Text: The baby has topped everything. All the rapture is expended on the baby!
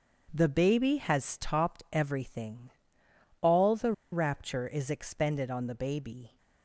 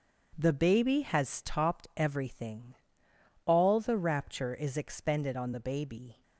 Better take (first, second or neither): second